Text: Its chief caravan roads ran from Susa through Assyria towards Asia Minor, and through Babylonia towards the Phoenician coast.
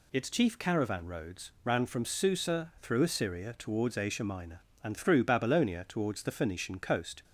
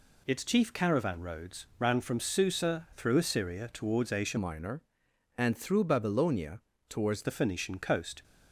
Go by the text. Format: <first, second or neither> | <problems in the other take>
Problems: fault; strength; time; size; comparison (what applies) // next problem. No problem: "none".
first | changes voice from "Minor" to "towards"; from 4.3 to 7.2 s; 2.9 s long // pauses between "Babylonia" and "towards"; slight; at 6.6 s; 0.28 s long